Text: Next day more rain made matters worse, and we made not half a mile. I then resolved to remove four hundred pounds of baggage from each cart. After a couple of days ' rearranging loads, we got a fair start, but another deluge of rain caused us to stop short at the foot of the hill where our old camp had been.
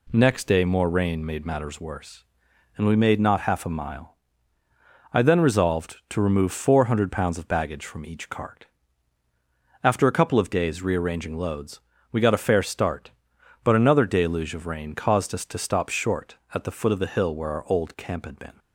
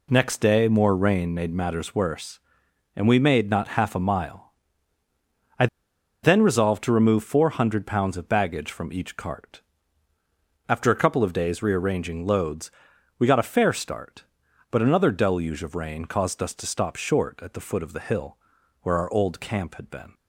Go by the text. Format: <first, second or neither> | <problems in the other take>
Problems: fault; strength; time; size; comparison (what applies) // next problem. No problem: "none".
first | pauses between "I" and "then"; noticeable; at 5.6 s; 0.55 s long // pauses between "hill" and "where"; noticeable; at 18.3 s; 0.46 s long